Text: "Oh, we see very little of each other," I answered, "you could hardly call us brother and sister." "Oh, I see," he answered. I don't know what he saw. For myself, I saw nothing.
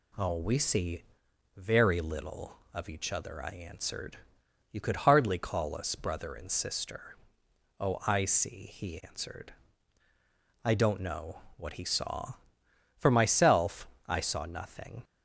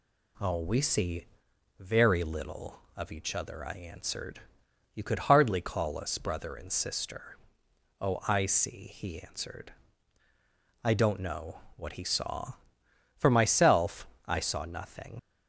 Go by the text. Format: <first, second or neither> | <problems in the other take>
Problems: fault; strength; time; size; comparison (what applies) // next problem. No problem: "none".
first | pauses between "see" and "very"; noticeable; at 1.2 s; 0.52 s long; noticeable in the first // pauses between "know" and "what"; slight; at 11.6 s; 0.16 s long; slight in the first // leaves "nothing" unfinished; at 15.1 s; 35 ms